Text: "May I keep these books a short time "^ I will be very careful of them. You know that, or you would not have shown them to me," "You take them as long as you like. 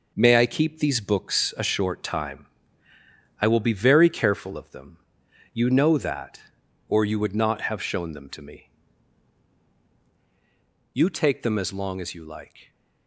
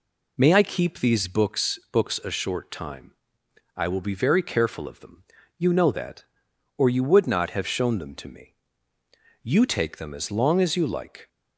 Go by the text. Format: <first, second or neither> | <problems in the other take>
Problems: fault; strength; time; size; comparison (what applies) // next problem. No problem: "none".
first | says "books" twice; at 1.9 s